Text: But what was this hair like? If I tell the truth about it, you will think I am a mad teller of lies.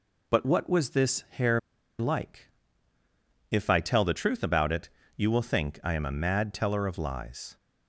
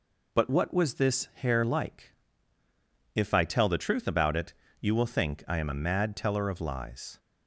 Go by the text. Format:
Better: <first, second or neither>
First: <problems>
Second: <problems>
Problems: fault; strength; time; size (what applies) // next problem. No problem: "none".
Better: second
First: pauses between "hair" and "like"; at 1.5 s; 0.39 s long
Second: none